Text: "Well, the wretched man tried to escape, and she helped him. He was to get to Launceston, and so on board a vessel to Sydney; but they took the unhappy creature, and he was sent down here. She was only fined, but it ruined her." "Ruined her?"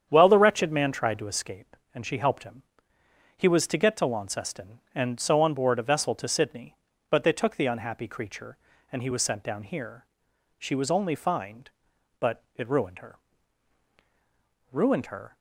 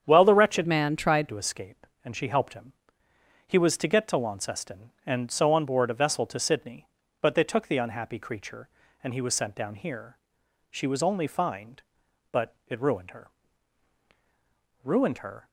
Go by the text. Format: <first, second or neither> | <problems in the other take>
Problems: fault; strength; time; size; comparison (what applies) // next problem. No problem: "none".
first | starts louder than the rest; strong; until 1.0 s; 8 dB; strong in the first // changes voice from "man" to "tried"; from 0.6 to 1.2 s; 0.6 s long